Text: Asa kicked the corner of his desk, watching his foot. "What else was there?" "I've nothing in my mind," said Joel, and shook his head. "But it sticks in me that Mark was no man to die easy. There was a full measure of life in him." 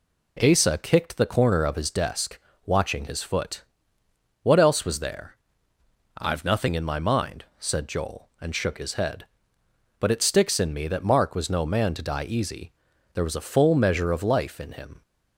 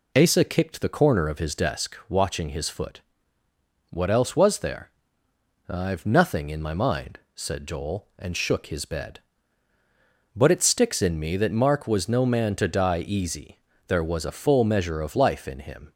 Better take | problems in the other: first | says "bed" for "head"; at 8.8 s

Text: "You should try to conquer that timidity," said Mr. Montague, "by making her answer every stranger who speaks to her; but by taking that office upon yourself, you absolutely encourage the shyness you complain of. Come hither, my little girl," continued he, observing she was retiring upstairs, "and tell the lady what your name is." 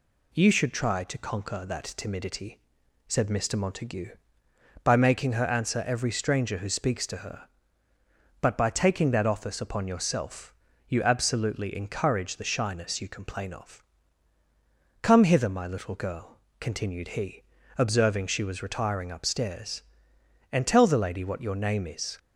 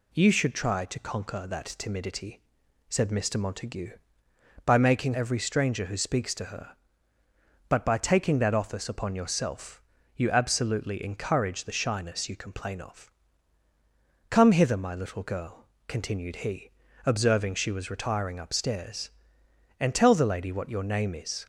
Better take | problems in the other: first | skips "her answer"; at 5.1 s

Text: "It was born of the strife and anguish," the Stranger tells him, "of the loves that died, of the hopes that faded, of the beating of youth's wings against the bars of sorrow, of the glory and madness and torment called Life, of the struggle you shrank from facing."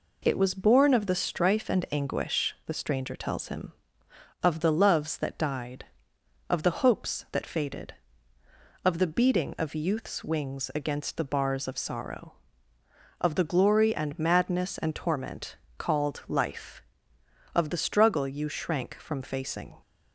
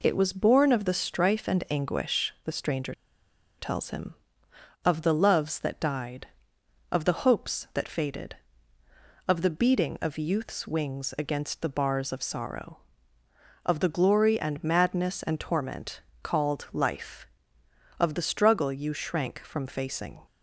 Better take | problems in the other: first | pauses between "Stranger" and "tells"; noticeable; at 2.9 s; 0.66 s long // pauses between "torment" and "called"; slight; at 16.0 s; 0.22 s long; slight in the first

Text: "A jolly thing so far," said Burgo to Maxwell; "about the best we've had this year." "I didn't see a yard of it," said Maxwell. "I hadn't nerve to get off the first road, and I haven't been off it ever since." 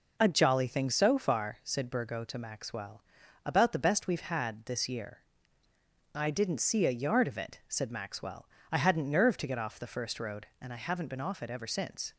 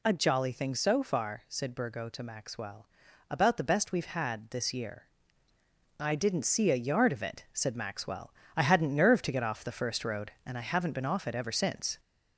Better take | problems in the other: first | gets louder; slight; throughout; 3 dB

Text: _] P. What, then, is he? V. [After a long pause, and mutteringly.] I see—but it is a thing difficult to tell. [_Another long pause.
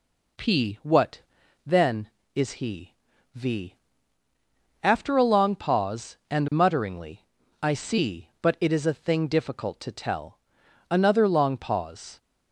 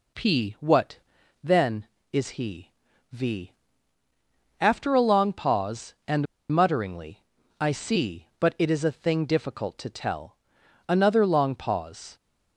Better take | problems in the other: first | pauses between "and" and "mutteringly"; slight; at 6.2 s; 0.25 s long

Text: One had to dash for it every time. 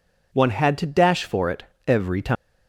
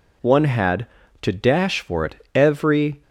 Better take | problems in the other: first | pauses between "it" and "every"; slight; at 2.1 s; 0.18 s long; slight in the first // stops before "time"; at 3.0 s

